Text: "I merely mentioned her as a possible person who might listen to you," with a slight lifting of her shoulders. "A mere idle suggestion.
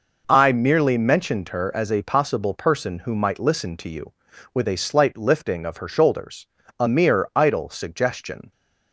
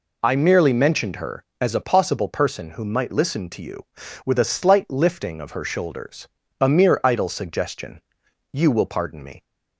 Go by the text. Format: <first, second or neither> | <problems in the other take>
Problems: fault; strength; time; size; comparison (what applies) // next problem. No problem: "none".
first | goes on to say "You will pardon me"; noticeable; from 8.4 s on; 0.94 s long